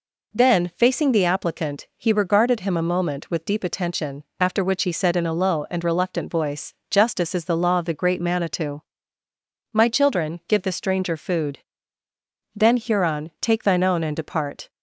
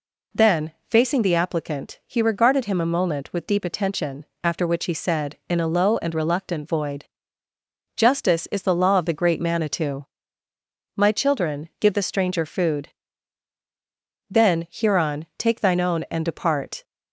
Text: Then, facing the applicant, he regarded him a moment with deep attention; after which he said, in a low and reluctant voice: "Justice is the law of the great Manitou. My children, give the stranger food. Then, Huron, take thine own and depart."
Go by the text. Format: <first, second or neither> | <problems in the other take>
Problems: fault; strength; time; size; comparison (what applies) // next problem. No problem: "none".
first | says "void" for "voice"; at 6.6 s